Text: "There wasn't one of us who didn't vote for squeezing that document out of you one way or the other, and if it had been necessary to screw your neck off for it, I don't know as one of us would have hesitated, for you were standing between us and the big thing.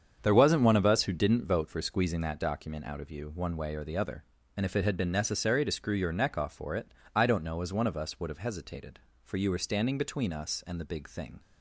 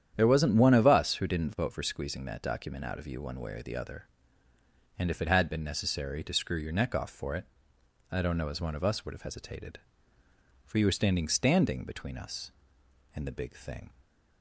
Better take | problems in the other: first | starts louder than the rest; strong; until 1.1 s; 9.5 dB; strong in the first // says "standing" twice; at 11.2 s

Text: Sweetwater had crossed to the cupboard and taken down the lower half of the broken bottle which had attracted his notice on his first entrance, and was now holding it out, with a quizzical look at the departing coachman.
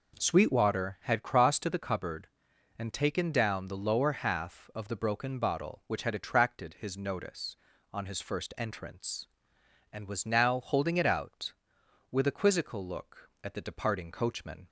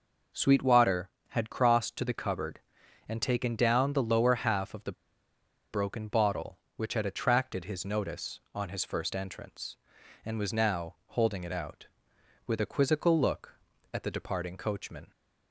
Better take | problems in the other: first | pauses between "the" and "broken"; noticeable; at 4.9 s; 0.78 s long

